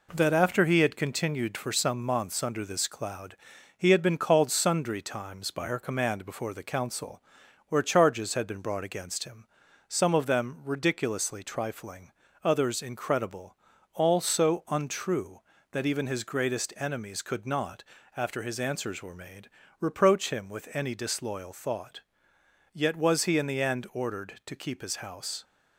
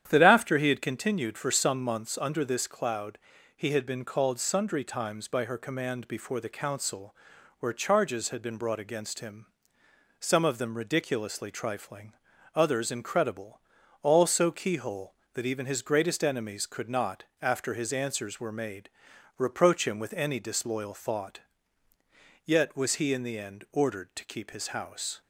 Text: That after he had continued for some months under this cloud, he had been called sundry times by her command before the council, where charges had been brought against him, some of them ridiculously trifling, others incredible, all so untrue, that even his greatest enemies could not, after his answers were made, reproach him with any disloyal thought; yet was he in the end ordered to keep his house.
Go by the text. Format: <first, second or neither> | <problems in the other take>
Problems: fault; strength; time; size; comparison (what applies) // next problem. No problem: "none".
first | starts louder than the rest; strong; until 1.1 s; 10 dB // says "keyhole" for "untrue"; at 14.5 s